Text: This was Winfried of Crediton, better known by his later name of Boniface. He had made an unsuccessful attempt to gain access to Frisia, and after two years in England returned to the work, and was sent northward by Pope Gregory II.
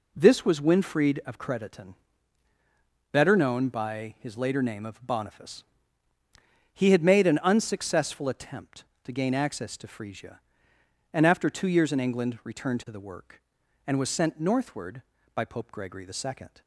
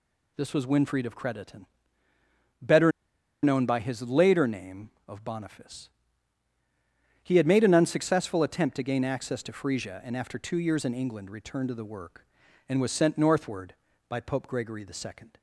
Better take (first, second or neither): first